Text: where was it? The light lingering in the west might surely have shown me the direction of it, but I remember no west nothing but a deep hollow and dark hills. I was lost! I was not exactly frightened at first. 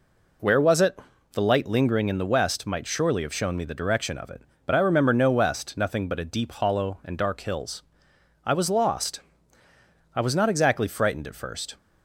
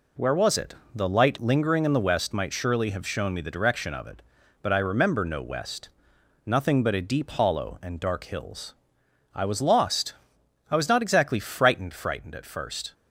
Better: first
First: none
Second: pauses between "west" and "nothing"; noticeable; at 5.8 s; 0.60 s long // says "frightened" twice; at 11.9 s

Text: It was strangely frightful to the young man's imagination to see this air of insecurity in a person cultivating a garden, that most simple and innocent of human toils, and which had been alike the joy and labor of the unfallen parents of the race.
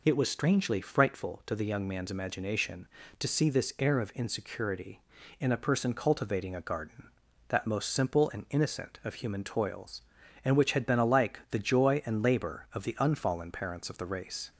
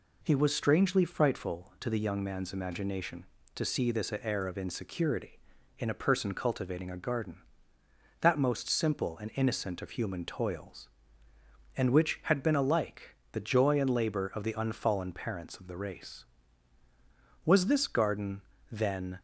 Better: first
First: none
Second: pauses between "alike" and "the"; slight; at 13.1 s; 0.16 s long // goes on to say "Was this garden then"; strong; from 17.4 s on; 1.7 s long

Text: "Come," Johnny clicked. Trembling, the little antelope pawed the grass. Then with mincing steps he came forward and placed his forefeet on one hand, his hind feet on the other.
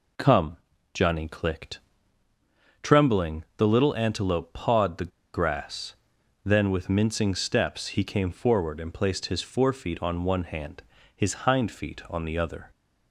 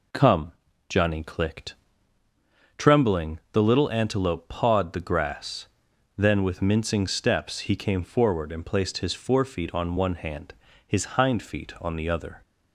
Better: second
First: pauses between "the" and "grass"; slight; at 5.1 s; 0.23 s long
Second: none

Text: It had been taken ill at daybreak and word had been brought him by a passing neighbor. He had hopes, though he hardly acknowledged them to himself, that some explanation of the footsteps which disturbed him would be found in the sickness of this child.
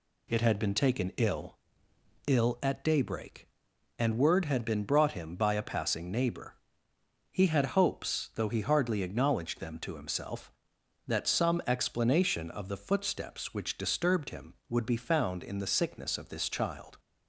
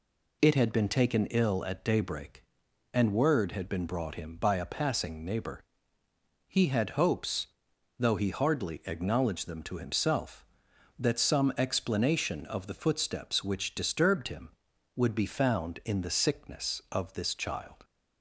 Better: second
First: says "ill" twice; at 2.2 s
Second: none

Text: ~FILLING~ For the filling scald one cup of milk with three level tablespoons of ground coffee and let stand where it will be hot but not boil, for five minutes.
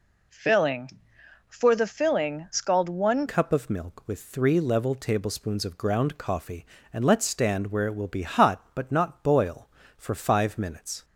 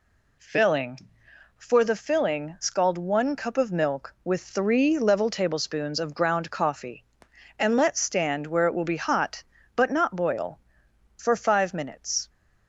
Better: second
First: changes voice at "cup"; from 3.2 s on; 7.8 s long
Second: none

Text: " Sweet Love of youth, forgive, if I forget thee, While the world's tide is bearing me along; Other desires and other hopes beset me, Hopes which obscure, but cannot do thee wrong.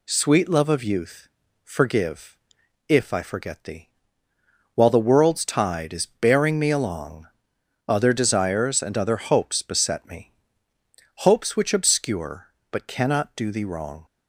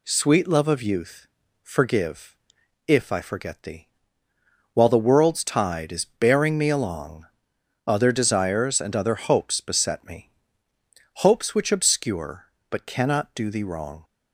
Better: neither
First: none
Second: none

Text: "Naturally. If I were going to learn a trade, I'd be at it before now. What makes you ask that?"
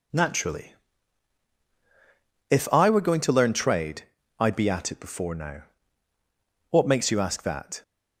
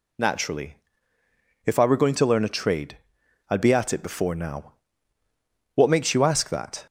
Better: second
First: skips "a"; at 3.5 s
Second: none

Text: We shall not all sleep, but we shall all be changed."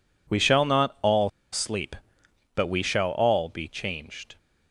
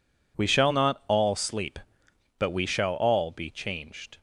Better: second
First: pauses between "all" and "sleep"; slight; at 1.2 s; 0.22 s long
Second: none

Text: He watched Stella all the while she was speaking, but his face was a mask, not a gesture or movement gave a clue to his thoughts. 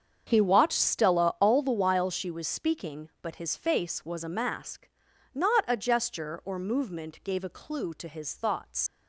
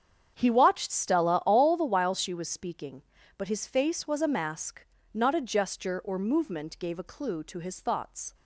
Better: second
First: starts louder than the rest; strong; until 1.2 s; 7.5 dB // leaves "thoughts" unfinished; at 8.8 s; 110 ms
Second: starts louder than the rest; strong; until 1.3 s; 8 dB

